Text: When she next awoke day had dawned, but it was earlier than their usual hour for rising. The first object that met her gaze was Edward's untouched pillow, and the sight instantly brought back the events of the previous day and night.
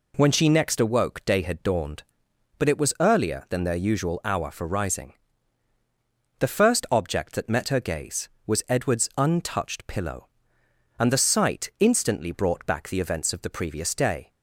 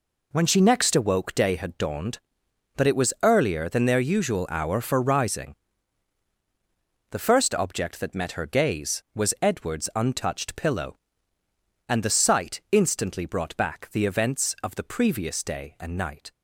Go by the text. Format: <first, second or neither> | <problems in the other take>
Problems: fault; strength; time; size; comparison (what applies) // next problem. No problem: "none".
second | stops before "and night"; at 14.3 s